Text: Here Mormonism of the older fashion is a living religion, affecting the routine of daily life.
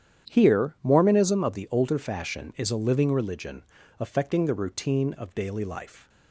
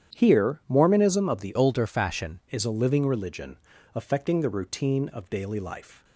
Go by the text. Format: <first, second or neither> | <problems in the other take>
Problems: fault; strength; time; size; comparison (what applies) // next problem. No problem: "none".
first | starts louder than the rest; strong; until 1.2 s; 9.5 dB; strong in the first // changes voice from "older" to "fashion"; from 1.5 to 2.4 s; 0.9 s long